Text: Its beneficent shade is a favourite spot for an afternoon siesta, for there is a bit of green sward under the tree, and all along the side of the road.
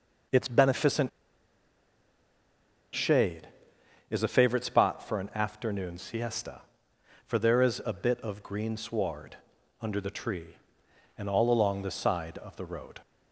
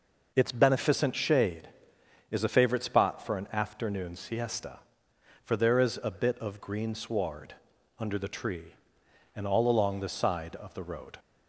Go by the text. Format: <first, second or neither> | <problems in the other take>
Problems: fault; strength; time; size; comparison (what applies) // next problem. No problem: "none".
second | pauses between "beneficent" and "shade"; strong; at 1.0 s; 1.8 s long // pauses between "sward" and "under"; at 9.3 s; 0.44 s long; also in the second